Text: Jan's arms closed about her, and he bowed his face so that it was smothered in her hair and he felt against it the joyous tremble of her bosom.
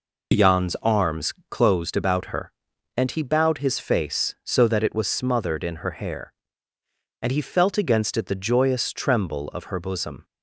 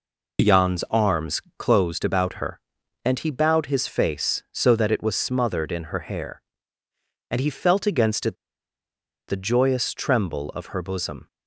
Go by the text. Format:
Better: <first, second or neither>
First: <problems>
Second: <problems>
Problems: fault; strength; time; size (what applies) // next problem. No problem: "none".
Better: first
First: pauses between "arms" and "closed"; slight; at 1.3 s; 0.18 s long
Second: pauses between "arms" and "closed"; slight; at 1.4 s; 0.18 s long // pauses between "it" and "the"; noticeable; at 8.3 s; 0.93 s long